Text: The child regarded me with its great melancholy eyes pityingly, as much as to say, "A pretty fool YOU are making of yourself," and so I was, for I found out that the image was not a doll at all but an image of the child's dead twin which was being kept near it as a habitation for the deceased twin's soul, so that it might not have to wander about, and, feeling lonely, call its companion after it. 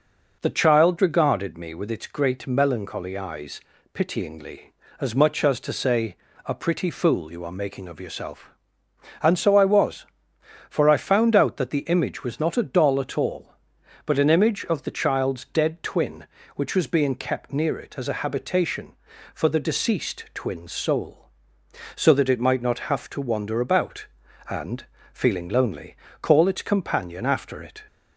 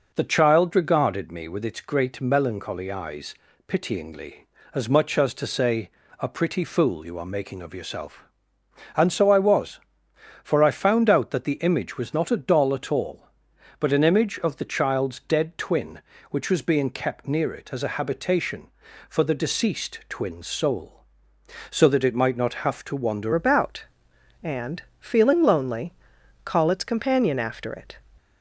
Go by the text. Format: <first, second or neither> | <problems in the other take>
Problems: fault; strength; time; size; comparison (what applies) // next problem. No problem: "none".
first | pauses between "eyes" and "pityingly"; slight; at 3.3 s; 0.32 s long; slight in the first // changes voice at "about"; from 23.3 s on; 4.6 s long